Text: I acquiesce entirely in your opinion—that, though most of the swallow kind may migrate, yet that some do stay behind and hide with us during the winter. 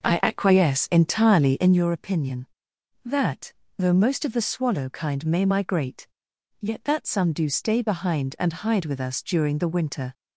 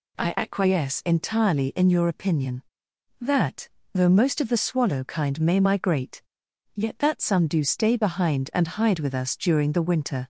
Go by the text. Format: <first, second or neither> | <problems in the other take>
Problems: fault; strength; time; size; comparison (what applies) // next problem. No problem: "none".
second | starts louder than the rest; noticeable; until 1.9 s; 5.5 dB